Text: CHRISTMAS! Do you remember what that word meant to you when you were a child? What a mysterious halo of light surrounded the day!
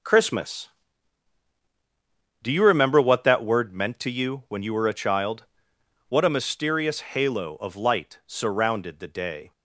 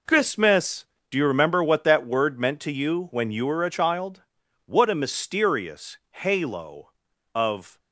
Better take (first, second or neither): first